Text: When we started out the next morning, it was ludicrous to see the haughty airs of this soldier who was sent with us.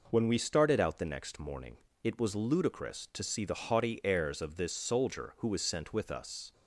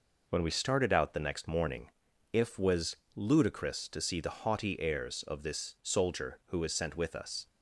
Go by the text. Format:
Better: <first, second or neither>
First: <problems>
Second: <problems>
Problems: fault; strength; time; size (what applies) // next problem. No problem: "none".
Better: first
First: none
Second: says "if" for "it"; at 2.3 s // pauses between "was" and "ludicrous"; slight; at 2.9 s; 0.20 s long